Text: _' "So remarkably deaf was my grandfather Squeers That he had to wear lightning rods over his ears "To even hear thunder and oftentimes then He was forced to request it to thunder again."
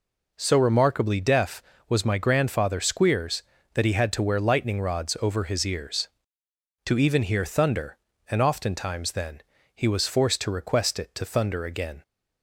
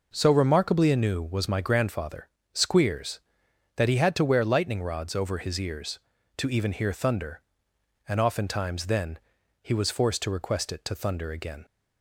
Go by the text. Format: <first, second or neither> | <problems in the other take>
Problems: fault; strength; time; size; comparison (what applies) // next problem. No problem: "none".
first | says "anew" for "deaf"; at 0.9 s // pauses between "grandfather" and "Squeers"; slight; at 2.2 s; 0.24 s long // pauses between "then" and "He"; at 9.1 s; 0.42 s long; slight in the first